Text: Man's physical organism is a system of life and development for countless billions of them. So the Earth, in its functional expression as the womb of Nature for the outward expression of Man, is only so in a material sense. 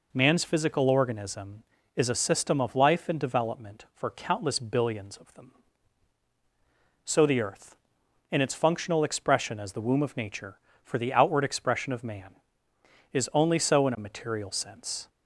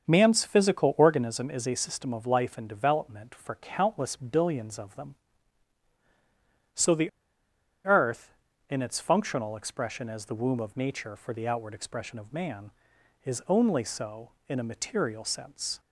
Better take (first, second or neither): first